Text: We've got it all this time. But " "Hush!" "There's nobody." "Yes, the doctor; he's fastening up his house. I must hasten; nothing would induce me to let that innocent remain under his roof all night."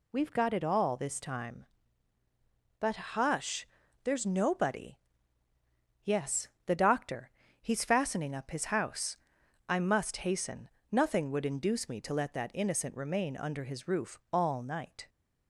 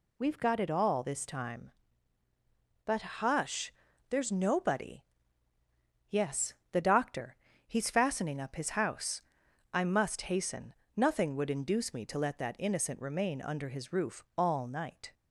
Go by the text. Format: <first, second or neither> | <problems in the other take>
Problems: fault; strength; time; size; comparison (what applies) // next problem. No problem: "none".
neither | none